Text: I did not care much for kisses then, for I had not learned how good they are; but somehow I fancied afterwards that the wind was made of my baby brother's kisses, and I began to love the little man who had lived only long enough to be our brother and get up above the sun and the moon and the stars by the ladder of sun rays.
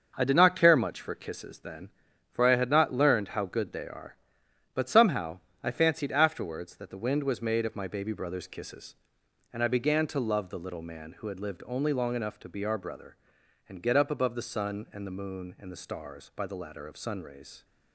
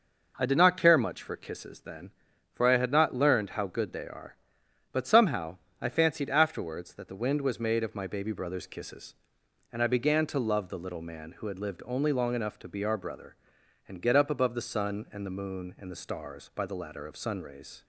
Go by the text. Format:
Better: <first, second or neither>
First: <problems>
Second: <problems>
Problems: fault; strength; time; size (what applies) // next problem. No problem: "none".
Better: second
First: gets quieter; throughout; 7 dB // pauses between "somehow" and "I"; slight; at 5.4 s; 0.20 s long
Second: pauses between "somehow" and "I"; slight; at 5.5 s; 0.20 s long